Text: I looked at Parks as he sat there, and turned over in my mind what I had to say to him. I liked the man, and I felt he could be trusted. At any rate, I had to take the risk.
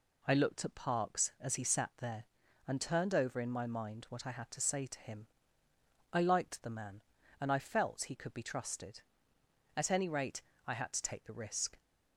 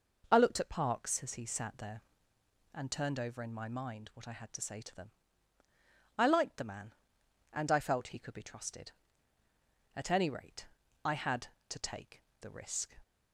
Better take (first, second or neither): first